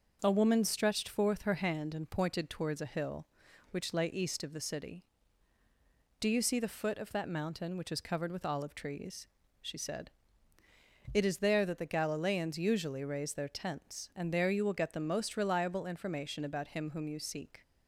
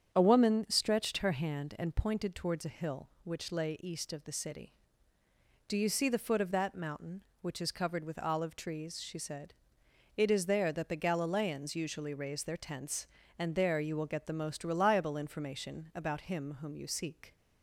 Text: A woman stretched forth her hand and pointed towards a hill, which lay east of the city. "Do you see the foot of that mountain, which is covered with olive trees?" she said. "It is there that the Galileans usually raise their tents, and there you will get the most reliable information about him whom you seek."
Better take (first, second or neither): first